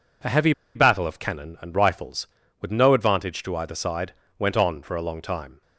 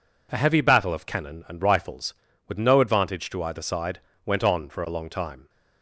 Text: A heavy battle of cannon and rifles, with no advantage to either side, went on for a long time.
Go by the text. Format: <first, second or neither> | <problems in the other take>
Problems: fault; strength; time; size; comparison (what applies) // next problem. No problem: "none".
second | pauses between "heavy" and "battle"; slight; at 0.5 s; 0.23 s long